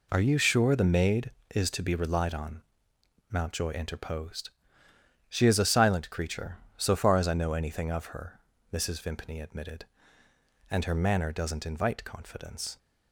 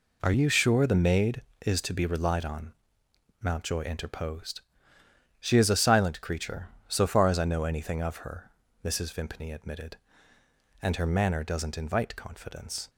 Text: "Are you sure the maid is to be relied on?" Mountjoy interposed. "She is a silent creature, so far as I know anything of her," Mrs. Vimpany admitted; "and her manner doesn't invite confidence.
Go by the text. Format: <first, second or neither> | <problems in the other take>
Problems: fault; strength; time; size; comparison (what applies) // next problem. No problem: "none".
neither | none